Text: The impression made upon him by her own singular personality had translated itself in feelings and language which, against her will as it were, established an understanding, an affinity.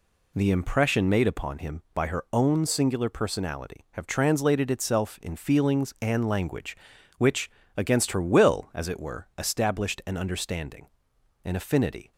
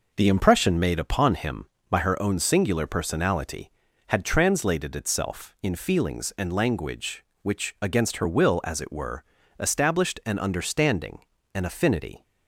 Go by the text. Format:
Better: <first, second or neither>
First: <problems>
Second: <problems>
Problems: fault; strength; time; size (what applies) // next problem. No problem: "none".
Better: second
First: says "have" for "had"; at 3.9 s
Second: none